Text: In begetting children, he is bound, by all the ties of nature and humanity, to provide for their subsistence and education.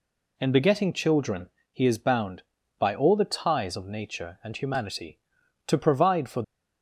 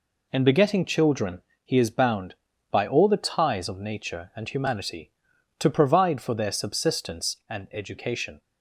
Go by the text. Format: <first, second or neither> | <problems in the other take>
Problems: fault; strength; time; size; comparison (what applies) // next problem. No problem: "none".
second | stops before "their subsistence and education"; at 6.4 s